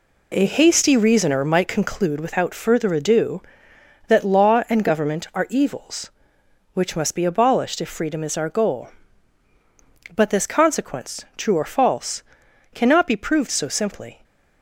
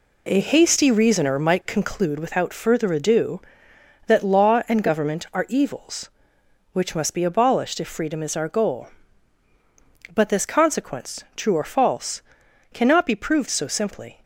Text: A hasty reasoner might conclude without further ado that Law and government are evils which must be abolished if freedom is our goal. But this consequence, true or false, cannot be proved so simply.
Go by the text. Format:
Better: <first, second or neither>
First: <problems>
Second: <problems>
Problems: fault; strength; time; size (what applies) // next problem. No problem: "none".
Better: neither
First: none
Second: none